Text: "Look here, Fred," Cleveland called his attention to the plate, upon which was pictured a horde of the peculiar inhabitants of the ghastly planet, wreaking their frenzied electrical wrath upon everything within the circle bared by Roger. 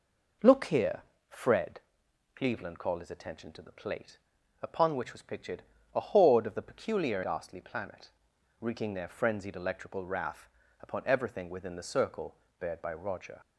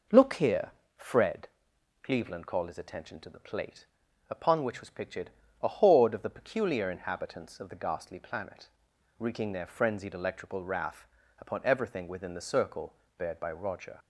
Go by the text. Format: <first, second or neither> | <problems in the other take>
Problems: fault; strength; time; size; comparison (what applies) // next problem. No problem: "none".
second | pauses between "pictured" and "a"; slight; at 5.6 s; 0.30 s long; slight in the second // skips "inhabitants of the"; at 7.2 s // pauses between "wrath" and "upon"; slight; at 10.5 s; 0.30 s long; slight in the second // pauses between "circle" and "bared"; slight; at 12.3 s; 0.22 s long; slight in the second